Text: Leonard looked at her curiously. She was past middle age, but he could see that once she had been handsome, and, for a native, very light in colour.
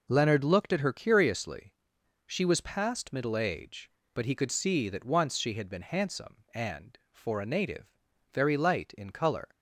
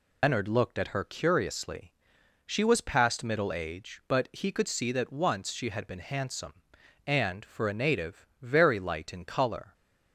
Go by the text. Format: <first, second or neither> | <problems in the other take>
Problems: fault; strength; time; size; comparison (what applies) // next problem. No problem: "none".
first | loses the start of "Leonard"; at 0.2 s; 135 ms